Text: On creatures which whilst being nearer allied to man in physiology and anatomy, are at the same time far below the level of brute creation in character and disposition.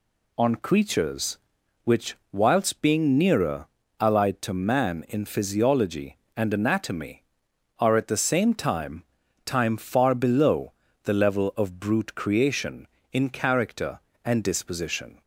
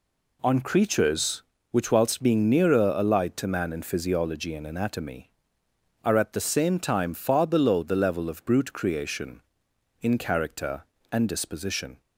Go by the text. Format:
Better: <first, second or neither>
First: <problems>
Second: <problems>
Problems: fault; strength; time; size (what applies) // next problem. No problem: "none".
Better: second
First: pauses between "which" and "whilst"; slight; at 2.1 s; 0.16 s long // pauses between "nearer" and "allied"; slight; at 3.6 s; 0.32 s long // says "time" twice; at 9.4 s // pauses between "below" and "the"; slight; at 10.7 s; 0.32 s long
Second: none